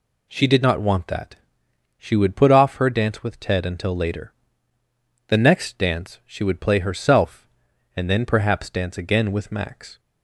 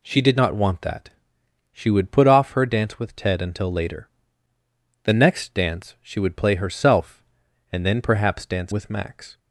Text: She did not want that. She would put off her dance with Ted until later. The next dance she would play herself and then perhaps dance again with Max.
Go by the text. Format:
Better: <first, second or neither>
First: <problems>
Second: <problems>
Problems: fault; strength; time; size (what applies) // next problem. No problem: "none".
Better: first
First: none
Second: skips "again"; at 8.7 s